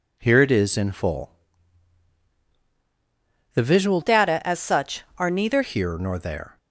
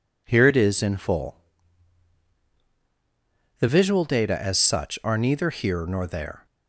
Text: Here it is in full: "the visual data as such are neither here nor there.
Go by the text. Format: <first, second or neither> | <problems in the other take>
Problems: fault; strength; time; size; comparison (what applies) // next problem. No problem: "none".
second | changes voice from "data" to "neither"; from 4.0 to 5.6 s; 1.6 s long